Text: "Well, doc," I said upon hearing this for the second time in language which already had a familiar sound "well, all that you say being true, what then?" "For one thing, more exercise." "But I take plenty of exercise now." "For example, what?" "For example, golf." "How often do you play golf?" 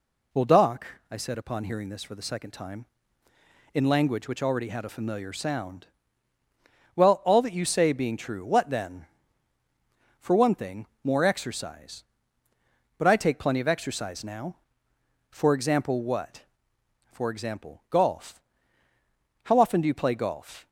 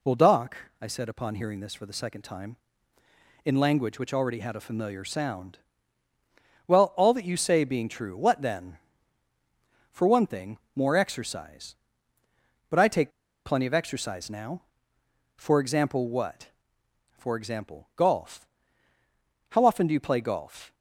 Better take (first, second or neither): first